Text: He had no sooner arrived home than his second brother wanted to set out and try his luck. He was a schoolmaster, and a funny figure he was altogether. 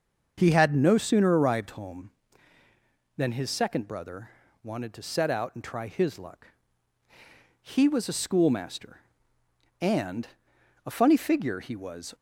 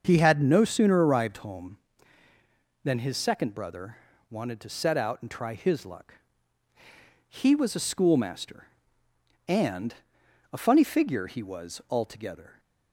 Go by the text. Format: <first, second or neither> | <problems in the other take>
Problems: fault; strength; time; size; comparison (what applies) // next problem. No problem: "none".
second | starts louder than the rest; until 1.3 s; 6.5 dB; also in the second // pauses between "brother" and "wanted"; slight; at 4.3 s; 0.32 s long; slight in the second // pauses between "and" and "a"; noticeable; at 10.2 s; 0.58 s long; noticeable in the second // stops before "altogether"; at 12.1 s